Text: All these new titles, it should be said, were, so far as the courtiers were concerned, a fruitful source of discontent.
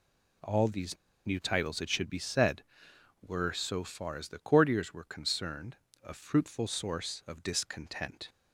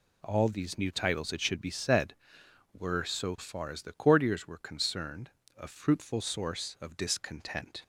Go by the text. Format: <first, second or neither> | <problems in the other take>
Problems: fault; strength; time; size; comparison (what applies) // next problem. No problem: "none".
second | pauses between "these" and "new"; slight; at 0.9 s; 0.30 s long